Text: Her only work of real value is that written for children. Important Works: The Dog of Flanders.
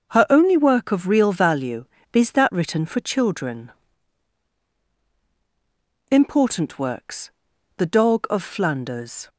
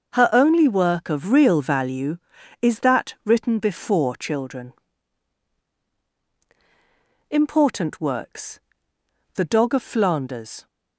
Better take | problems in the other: first | starts louder than the rest; noticeable; until 1.1 s; 6 dB; noticeable in the first // says "before" for "for"; at 3.6 s

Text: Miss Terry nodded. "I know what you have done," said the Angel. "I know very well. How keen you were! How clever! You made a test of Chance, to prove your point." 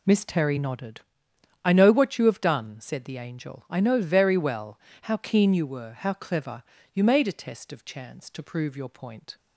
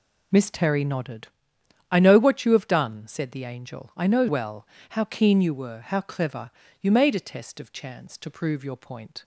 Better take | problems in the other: first | skips "very"; at 4.2 s

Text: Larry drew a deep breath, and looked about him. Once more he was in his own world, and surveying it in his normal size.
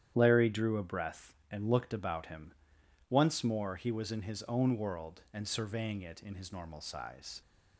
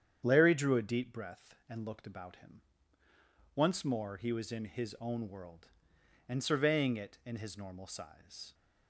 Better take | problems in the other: second | starts louder than the rest; strong; until 1.1 s; 10 dB; strong in the second // skips "deep"; at 0.8 s

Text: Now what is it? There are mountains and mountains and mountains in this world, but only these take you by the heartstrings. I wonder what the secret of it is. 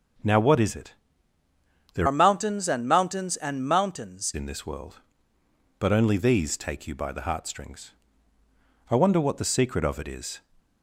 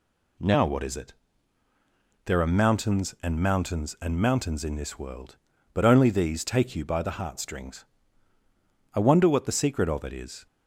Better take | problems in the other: second | starts louder than the rest; noticeable; until 2.2 s; 6 dB // changes voice from "are" to "mountains"; from 2.0 to 4.3 s; 2.3 s long

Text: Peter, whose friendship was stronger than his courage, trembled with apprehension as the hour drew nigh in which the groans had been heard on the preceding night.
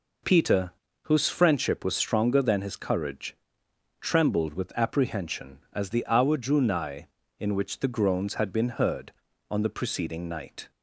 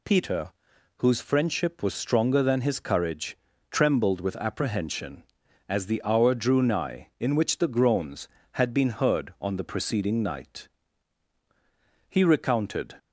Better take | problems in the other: first | goes on to say "He recounted"; noticeable; from 12.0 s on; 0.86 s long

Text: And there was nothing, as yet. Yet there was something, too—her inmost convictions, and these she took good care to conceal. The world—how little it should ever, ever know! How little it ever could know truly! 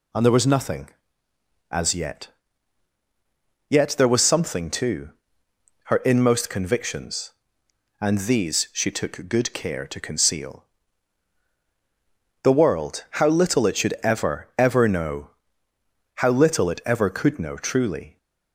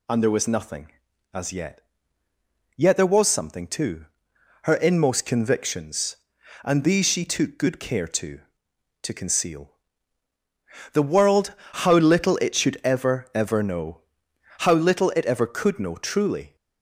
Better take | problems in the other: first | says "to" twice; at 9.0 s

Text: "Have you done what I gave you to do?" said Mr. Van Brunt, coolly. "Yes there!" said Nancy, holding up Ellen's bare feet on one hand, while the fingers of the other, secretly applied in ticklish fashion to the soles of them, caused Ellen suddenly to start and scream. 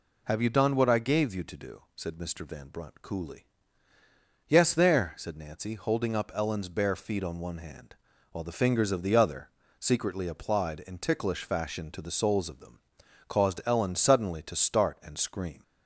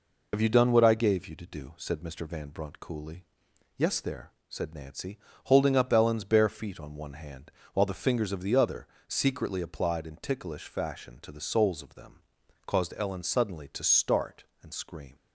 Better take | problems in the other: first | loses the start of "Have"; at 0.3 s; 70 ms

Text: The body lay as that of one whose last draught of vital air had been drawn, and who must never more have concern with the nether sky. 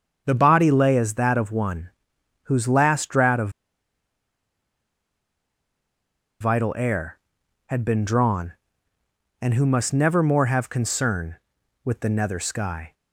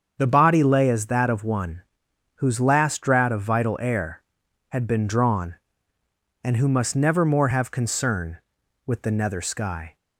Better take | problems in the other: second | starts louder than the rest; until 1.2 s; 7 dB; also in the second // pauses between "one" and "whose"; noticeable; at 1.8 s; 0.54 s long; noticeable in the second // pauses between "of" and "vital"; strong; at 3.4 s; 2.9 s long

